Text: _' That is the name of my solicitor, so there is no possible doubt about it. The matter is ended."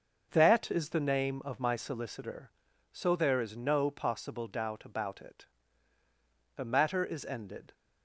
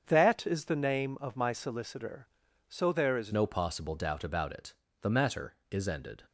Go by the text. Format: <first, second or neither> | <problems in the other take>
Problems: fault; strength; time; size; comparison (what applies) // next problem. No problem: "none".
first | starts louder than the rest; strong; until 1.0 s; 7 dB; noticeable in the first // changes voice at "no"; from 3.3 s on; 2.9 s long